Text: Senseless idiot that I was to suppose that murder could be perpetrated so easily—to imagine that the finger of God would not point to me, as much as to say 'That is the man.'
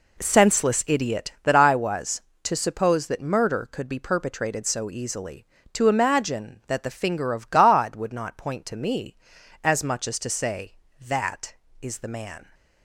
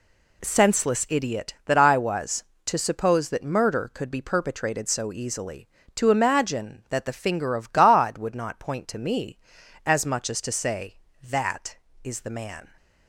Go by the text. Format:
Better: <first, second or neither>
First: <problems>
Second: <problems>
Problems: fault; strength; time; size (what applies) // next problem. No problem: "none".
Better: second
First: starts louder than the rest; slight; until 1.7 s; 3 dB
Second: none